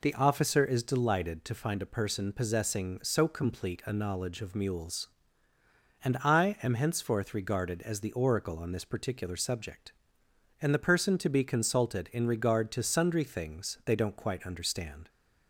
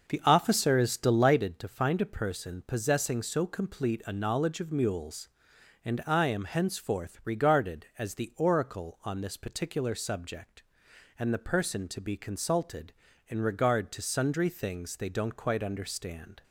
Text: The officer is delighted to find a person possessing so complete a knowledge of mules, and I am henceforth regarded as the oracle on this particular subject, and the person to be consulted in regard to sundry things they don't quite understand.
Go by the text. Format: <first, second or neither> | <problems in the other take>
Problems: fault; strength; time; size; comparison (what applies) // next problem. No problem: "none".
first | starts louder than the rest; noticeable; until 1.5 s; 6 dB